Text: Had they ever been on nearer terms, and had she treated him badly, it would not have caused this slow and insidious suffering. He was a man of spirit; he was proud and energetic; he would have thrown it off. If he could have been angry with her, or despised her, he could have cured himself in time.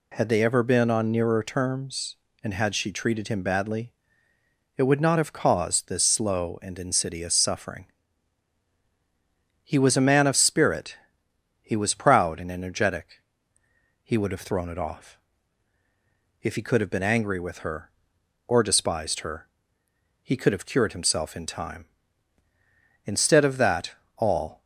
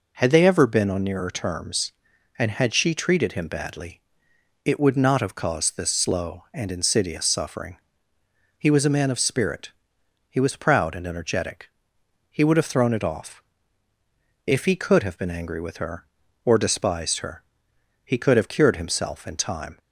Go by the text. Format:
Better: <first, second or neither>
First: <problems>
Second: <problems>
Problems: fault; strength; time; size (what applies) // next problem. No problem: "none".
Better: second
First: goes on to say "Instead of that all"; from 23.1 s on; 1.5 s long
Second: none